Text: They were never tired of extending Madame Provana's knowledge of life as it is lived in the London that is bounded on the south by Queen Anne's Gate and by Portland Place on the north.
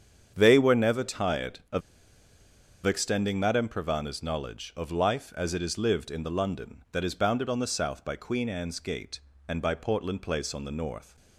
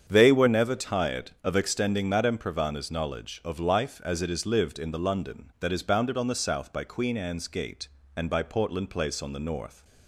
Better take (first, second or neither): second